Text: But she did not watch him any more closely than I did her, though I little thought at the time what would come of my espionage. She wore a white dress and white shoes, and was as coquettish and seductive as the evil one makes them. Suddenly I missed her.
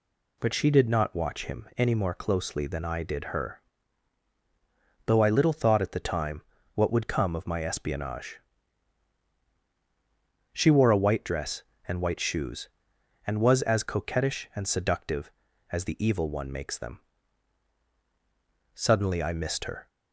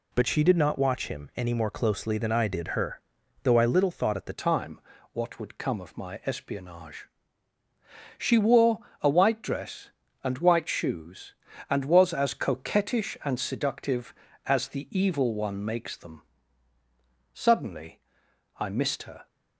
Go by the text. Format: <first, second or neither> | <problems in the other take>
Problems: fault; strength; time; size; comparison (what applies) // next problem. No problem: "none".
first | changes voice at "time"; from 4.3 s on; 14.9 s long // pauses between "time" and "what"; slight; at 4.8 s; 0.32 s long; slight in the first // pauses between "wore" and "a"; slight; at 8.8 s; 0.22 s long // pauses between "Suddenly" and "I"; noticeable; at 18.0 s; 0.58 s long